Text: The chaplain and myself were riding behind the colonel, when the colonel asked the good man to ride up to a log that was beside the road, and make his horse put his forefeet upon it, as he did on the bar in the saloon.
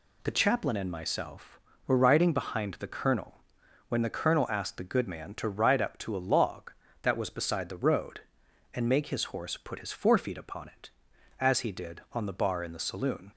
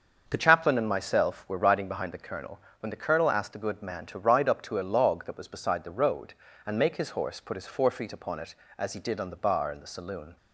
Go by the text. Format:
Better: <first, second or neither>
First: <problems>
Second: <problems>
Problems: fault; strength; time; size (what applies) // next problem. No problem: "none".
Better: first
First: none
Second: starts louder than the rest; until 1.3 s; 6.5 dB // changes voice at "chaplain"; from 0.3 s on; 10.0 s long